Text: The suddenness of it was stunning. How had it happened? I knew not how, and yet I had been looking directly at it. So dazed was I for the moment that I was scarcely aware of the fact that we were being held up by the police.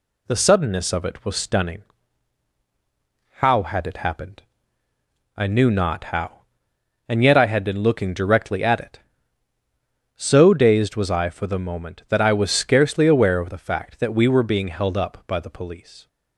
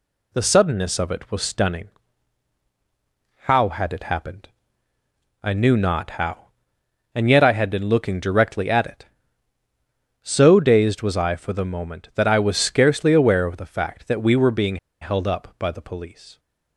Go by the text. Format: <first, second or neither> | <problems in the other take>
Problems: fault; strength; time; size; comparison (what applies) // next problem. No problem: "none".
first | pauses between "being" and "held"; slight; at 14.7 s; 0.24 s long